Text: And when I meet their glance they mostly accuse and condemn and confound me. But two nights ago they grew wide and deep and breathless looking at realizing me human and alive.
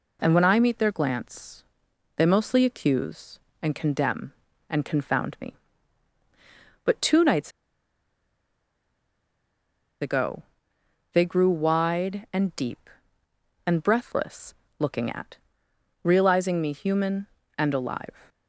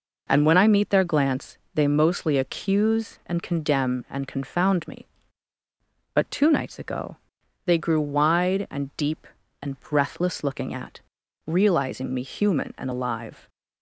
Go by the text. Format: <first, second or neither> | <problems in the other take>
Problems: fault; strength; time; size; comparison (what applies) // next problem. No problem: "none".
second | pauses between "glance" and "they"; noticeable; at 1.6 s; 0.52 s long; slight in the second // pauses between "nights" and "ago"; strong; at 7.5 s; 2.5 s long // pauses between "ago" and "they"; noticeable; at 10.4 s; 0.70 s long; noticeable in the second // pauses between "breathless" and "looking"; slight; at 14.5 s; 0.24 s long // pauses between "at" and "realizing"; noticeable; at 15.3 s; 0.68 s long; noticeable in the second